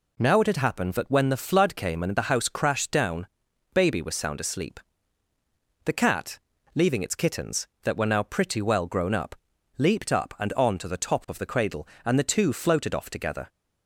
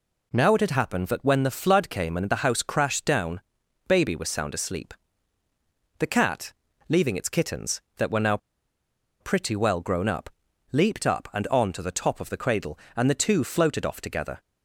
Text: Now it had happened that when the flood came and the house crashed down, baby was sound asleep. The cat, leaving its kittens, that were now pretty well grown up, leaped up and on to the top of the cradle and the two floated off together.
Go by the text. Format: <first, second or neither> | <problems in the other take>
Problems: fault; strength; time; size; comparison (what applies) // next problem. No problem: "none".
first | pauses between "now" and "pretty"; noticeable; at 8.3 s; 0.83 s long